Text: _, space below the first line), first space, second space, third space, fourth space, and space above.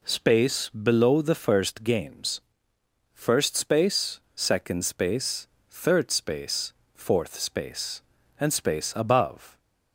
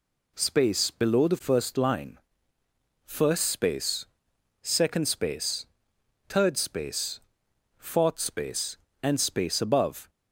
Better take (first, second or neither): second